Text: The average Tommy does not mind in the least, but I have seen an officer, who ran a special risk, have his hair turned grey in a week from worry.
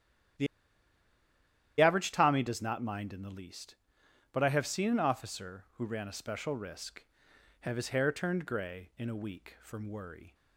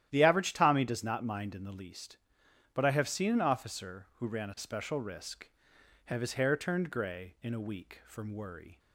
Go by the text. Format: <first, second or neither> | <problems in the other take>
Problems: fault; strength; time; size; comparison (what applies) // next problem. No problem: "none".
second | starts louder than the rest; strong; until 2.7 s; 11.5 dB; strong in the second // pauses between "The" and "average"; strong; at 0.4 s; 1.3 s long